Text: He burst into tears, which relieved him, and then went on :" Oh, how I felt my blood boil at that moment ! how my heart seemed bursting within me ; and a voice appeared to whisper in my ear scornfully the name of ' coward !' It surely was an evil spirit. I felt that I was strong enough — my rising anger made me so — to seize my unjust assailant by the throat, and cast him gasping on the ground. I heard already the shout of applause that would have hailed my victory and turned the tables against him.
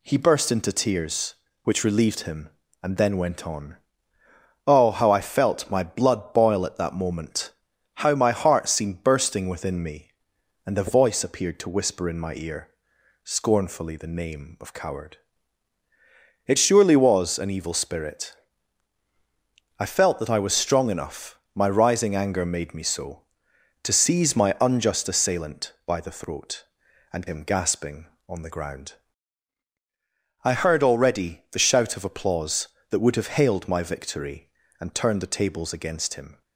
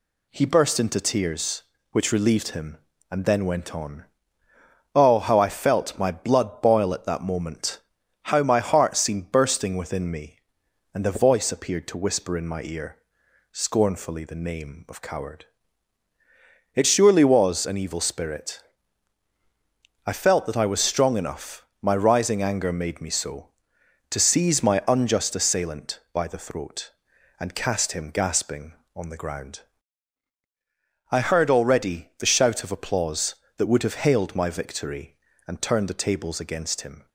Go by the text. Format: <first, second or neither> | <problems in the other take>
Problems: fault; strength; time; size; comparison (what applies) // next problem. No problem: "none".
second | pauses between "ear" and "scornfully"; noticeable; at 12.6 s; 0.54 s long; noticeable in the second // skips "cast"; at 27.2 s